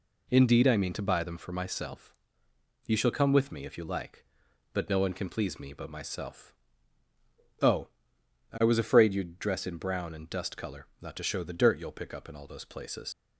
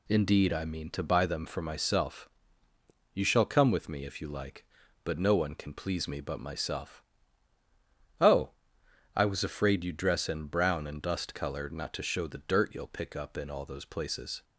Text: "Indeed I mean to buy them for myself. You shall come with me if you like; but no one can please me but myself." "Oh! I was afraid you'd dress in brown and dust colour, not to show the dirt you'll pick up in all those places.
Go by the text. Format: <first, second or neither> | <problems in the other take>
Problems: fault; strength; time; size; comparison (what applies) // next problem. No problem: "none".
second | leaves "places" unfinished; at 13.1 s; 85 ms